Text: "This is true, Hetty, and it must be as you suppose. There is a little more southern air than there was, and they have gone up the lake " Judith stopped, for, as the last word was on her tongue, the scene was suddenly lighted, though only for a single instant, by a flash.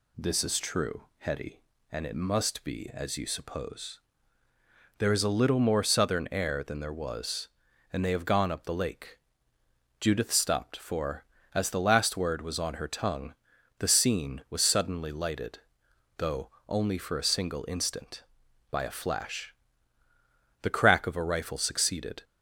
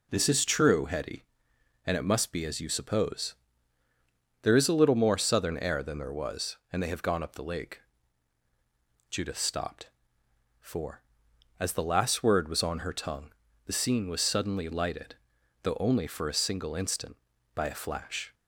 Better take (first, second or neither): second